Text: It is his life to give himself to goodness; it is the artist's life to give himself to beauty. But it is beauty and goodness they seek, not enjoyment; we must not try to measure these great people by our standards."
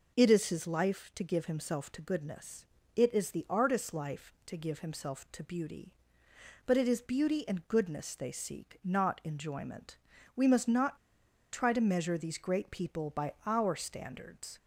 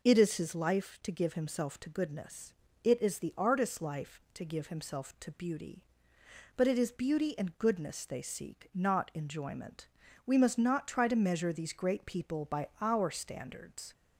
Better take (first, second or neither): second